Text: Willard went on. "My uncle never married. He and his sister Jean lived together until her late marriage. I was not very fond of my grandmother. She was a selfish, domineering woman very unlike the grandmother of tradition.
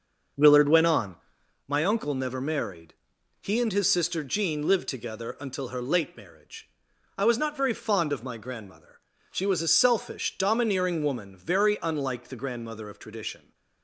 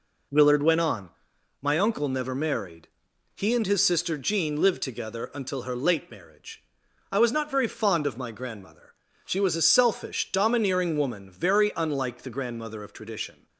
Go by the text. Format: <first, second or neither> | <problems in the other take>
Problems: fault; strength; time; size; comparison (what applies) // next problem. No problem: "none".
second | starts louder than the rest; until 1.6 s; 6 dB